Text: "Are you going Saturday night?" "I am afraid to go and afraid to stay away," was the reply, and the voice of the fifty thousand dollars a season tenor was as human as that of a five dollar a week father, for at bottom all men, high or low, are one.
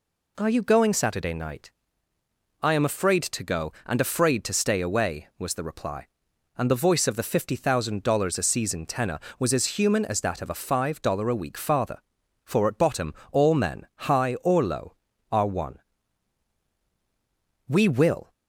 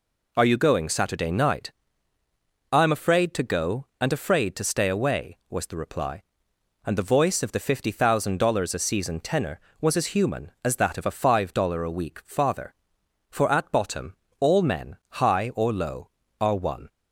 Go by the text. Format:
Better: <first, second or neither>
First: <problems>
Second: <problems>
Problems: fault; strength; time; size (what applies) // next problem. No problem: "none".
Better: second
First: pauses between "bottom" and "all"; slight; at 13.1 s; 0.18 s long // goes on to say "We will"; noticeable; from 17.6 s on; 0.64 s long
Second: pauses between "bottom" and "all"; slight; at 14.1 s; 0.24 s long